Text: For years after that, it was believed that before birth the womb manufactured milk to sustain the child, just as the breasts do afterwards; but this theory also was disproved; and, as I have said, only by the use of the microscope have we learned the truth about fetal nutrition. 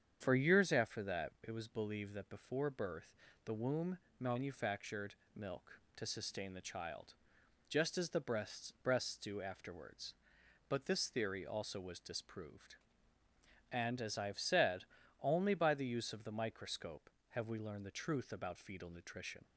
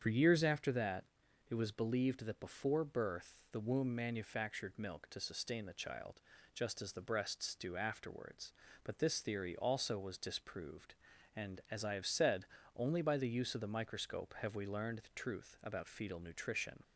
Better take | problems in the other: second | starts louder than the rest; strong; until 1.2 s; 8 dB; strong in the second // pauses between "birth" and "the"; slight; at 3.1 s; 0.30 s long; slight in the second // pauses between "womb" and "manufactured"; slight; at 3.9 s; 0.22 s long // pauses between "manufactured" and "milk"; slight; at 5.1 s; 0.20 s long // says "breasts" twice; at 8.8 s

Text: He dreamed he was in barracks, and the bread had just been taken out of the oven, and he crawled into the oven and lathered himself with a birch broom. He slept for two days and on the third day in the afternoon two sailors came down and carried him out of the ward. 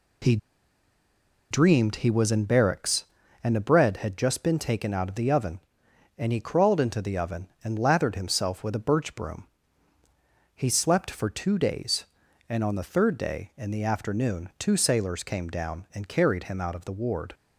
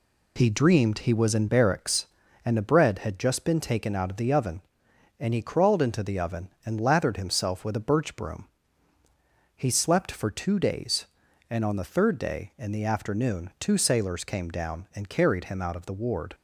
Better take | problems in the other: second | pauses between "He" and "dreamed"; at 0.3 s; 1.1 s long

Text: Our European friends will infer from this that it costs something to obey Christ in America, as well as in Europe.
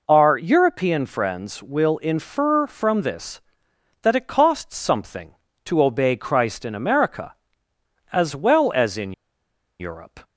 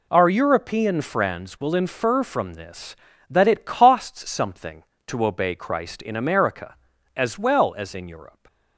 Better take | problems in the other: second | pauses between "in" and "Europe"; noticeable; at 9.1 s; 0.67 s long

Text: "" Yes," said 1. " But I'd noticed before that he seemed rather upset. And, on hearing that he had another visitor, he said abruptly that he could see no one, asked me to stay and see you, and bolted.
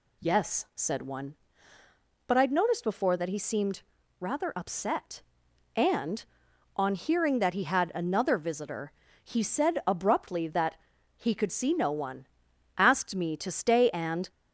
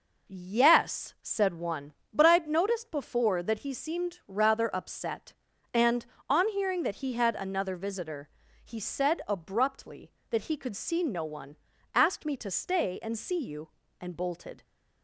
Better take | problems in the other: second | pauses between "seemed" and "rather"; slight; at 3.8 s; 0.36 s long // pauses between "that" and "he"; at 10.7 s; 0.40 s long // stops before "see you and bolted"; at 14.3 s

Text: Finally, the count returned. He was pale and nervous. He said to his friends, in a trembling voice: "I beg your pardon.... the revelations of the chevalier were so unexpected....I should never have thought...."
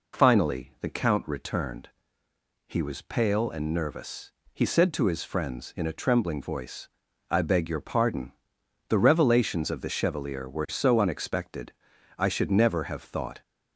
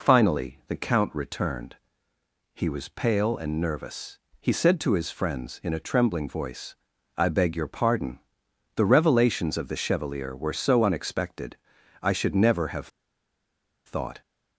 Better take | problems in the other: first | pauses between "have" and "thought"; at 12.8 s; 0.98 s long

